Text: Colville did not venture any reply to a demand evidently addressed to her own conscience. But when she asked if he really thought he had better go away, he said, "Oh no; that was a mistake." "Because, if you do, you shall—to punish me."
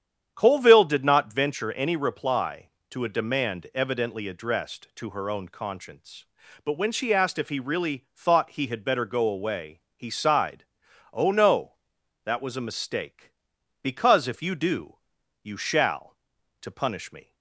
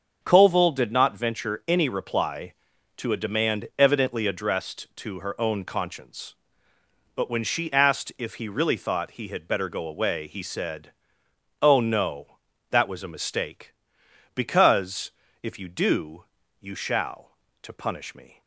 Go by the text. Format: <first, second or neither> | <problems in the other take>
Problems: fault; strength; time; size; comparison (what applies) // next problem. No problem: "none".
second | starts louder than the rest; strong; until 1.3 s; 9 dB; also in the second // says "sighed" for "said"; at 10.1 s